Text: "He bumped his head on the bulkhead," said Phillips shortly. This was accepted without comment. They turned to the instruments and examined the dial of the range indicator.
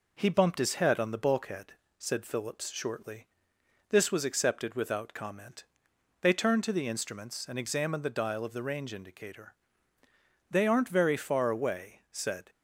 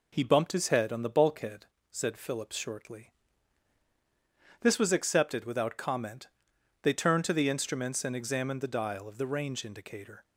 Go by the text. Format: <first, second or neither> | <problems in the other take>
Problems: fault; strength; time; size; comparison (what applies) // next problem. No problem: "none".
second | goes on to say "They aren't very far away said"; strong; from 10.4 s on; 2.0 s long